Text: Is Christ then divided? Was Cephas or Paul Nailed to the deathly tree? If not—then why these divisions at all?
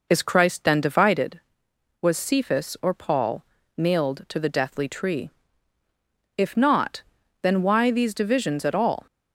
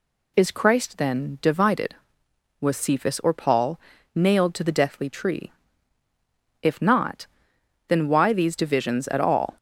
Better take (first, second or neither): second